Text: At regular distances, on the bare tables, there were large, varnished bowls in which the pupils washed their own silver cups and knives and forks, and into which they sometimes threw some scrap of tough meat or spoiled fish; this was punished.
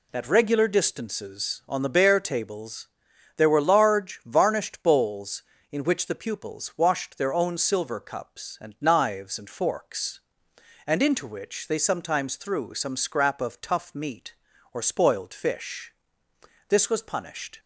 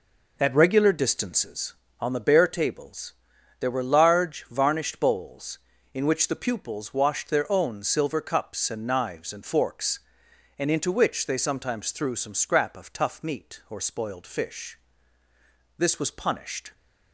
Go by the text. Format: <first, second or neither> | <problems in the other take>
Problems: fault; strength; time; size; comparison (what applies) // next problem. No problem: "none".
first | starts louder than the rest; noticeable; until 1.5 s; 4.5 dB